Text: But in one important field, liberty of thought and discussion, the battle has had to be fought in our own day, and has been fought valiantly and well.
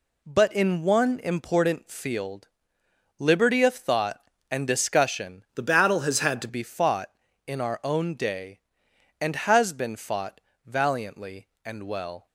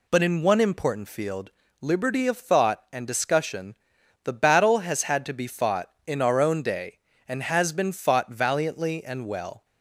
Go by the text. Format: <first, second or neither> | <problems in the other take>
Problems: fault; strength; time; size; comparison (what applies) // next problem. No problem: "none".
second | changes voice from "the" to "to"; from 5.5 to 6.4 s; 0.9 s long // pauses between "fought" and "valiantly"; slight; at 10.3 s; 0.26 s long